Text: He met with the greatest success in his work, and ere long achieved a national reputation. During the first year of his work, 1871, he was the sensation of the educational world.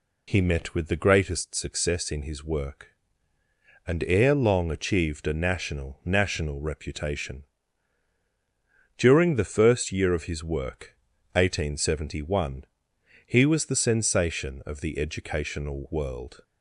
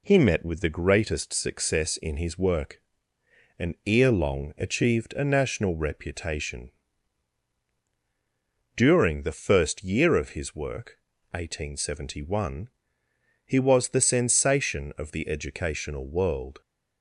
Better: second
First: says "national" twice; at 6.0 s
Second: none

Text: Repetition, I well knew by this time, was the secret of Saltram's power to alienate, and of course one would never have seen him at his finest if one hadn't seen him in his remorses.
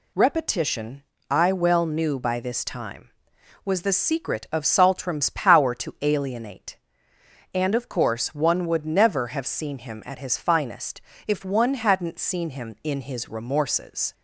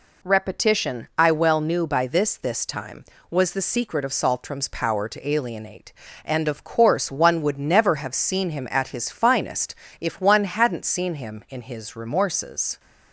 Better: first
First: pauses between "finest" and "if"; slight; at 10.9 s; 0.30 s long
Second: says "this" twice; at 2.3 s // pauses between "finest" and "if"; slight; at 9.7 s; 0.24 s long

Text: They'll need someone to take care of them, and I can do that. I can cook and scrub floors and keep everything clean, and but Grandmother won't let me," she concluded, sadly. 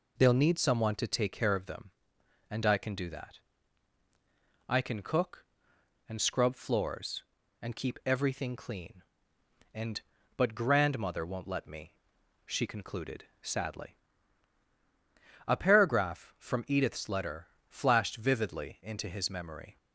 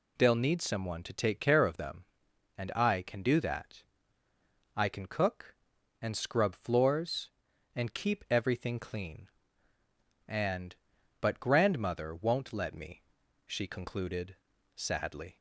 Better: second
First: goes on to say "A paragraph from Edith's letter flashed vividly into his memory"; strong; from 15.4 s on; 4.3 s long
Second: none

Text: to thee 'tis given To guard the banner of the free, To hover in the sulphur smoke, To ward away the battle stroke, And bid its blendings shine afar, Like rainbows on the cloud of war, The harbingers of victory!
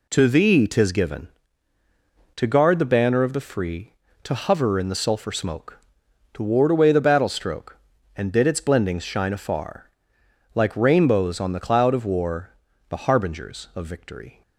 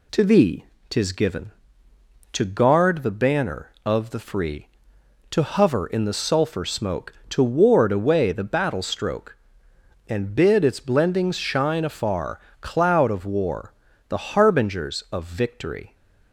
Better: first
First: none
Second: pauses between "thee" and "tis"; slight; at 0.6 s; 0.24 s long // skips "Like rainbows on the"; at 12.5 s

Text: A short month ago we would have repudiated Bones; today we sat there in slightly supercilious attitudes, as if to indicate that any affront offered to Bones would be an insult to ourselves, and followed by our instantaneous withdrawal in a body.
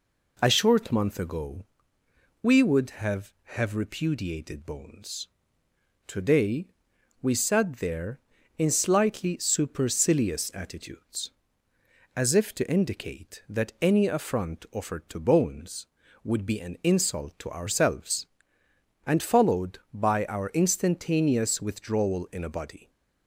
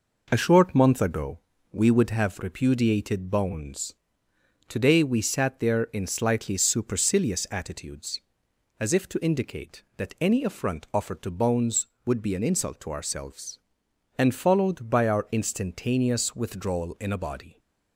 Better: second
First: pauses between "ago" and "we"; noticeable; at 1.6 s; 0.80 s long // says "have" twice; at 3.5 s // pauses between "today" and "we"; noticeable; at 6.6 s; 0.52 s long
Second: pauses between "ago" and "we"; slight; at 1.3 s; 0.34 s long

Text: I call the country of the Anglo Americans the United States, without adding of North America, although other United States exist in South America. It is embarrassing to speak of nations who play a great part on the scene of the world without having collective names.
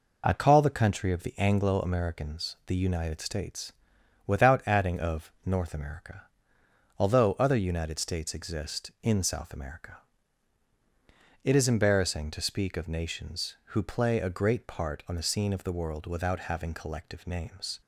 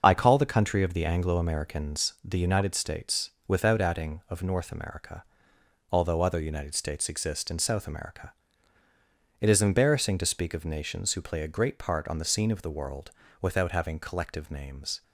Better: first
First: none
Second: loses the start of "I"; at 0.0 s; 25 ms // starts louder than the rest; until 1.0 s; 6.5 dB // pauses between "world" and "without"; slight; at 13.1 s; 0.28 s long

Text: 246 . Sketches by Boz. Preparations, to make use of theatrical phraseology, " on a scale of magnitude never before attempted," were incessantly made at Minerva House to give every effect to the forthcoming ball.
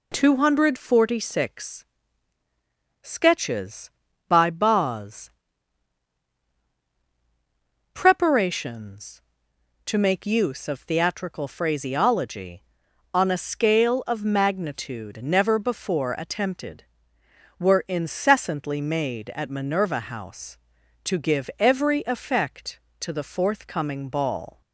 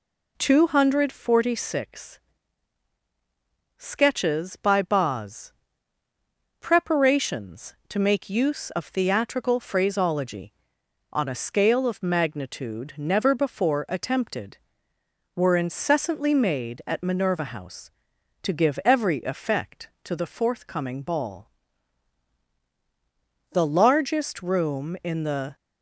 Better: first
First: none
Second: goes on to say "The largest room in the"; strong; from 23.5 s on; 2.0 s long

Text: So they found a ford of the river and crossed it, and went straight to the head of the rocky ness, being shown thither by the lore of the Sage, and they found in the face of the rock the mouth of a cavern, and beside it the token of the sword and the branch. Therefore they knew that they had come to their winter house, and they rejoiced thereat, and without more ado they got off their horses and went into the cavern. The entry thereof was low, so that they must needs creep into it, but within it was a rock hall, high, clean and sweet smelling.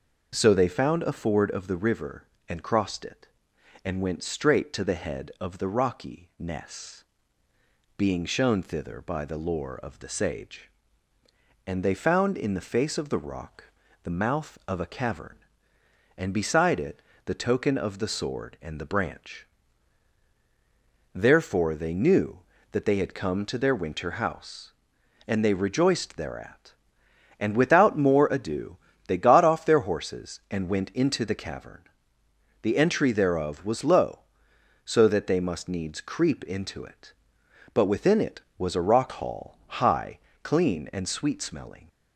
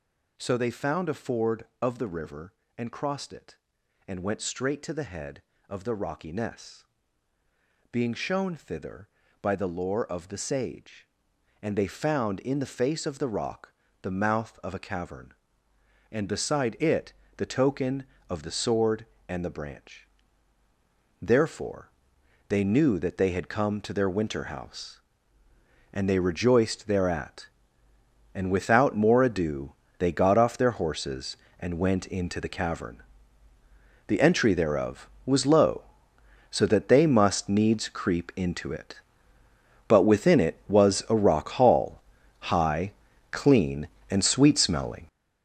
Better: first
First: pauses between "rock" and "the"; slight; at 13.6 s; 0.36 s long // pauses between "it" and "the"; slight; at 16.9 s; 0.26 s long // pauses between "ado" and "they"; slight; at 28.7 s; 0.28 s long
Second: gets louder; strong; throughout; 9.5 dB // pauses between "rock" and "the"; slight; at 13.7 s; 0.32 s long // pauses between "it" and "the"; slight; at 17.1 s; 0.24 s long // pauses between "Therefore" and "they"; noticeable; at 21.8 s; 0.60 s long // pauses between "ado" and "they"; slight; at 29.7 s; 0.26 s long

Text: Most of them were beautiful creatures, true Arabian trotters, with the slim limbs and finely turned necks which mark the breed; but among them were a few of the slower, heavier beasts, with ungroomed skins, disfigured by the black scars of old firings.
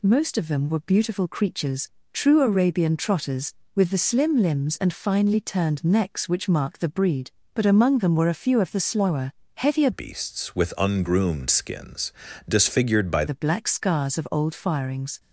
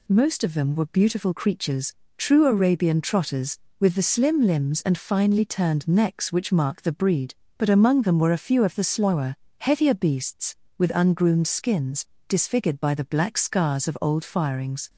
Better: second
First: changes voice from "beasts" to "by"; from 9.9 to 13.2 s; 3.3 s long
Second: none

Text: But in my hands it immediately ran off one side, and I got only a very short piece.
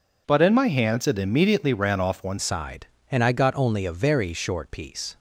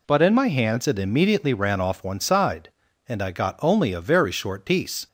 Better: second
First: changes voice at "side"; from 2.3 s on; 2.8 s long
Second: none

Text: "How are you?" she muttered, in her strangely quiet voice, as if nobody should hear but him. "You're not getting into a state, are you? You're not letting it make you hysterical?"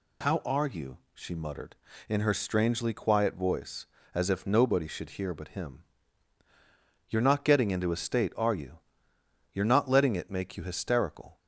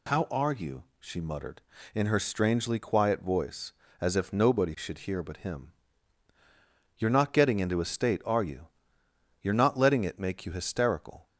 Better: neither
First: none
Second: none

